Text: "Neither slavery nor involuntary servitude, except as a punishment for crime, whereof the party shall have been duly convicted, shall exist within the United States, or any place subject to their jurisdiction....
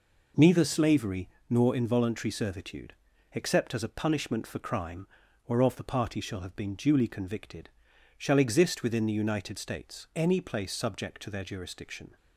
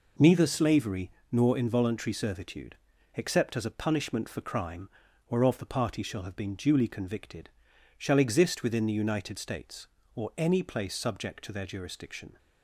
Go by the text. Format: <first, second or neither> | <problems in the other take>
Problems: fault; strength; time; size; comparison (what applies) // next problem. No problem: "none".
second | pauses between "slavery" and "nor"; slight; at 1.2 s; 0.20 s long; slight in the second // skips "or"; at 10.1 s